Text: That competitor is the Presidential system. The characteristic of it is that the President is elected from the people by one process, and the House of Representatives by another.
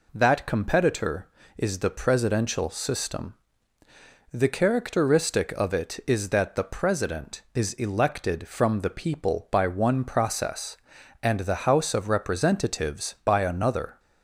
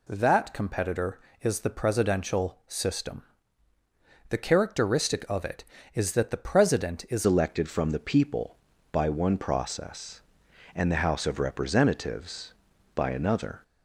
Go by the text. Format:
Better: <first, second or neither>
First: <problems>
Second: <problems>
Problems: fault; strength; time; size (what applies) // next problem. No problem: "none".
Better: first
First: none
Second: changes voice at "elected"; from 7.2 s on; 6.4 s long